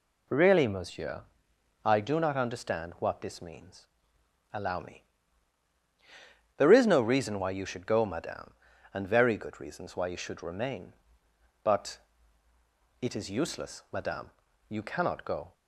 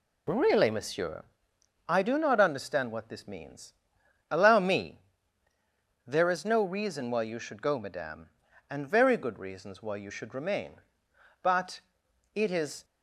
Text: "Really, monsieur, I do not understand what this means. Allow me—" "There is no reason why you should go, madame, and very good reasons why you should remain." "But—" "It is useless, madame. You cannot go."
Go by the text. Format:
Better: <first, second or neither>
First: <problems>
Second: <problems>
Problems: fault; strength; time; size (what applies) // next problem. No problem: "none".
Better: first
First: none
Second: stops before "useless madame You cannot go"; at 12.8 s